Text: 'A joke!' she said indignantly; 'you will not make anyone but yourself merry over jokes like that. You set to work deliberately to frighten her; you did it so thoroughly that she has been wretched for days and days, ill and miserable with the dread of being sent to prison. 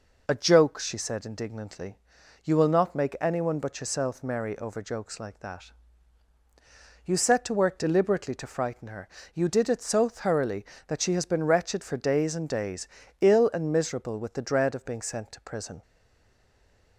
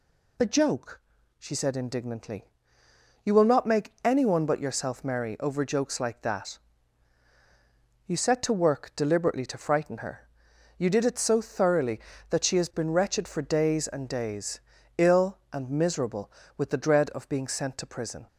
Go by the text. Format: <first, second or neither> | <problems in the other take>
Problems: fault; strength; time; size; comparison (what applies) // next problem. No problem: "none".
second | stays silent after the last word; from 15.8 s on; 1.1 s long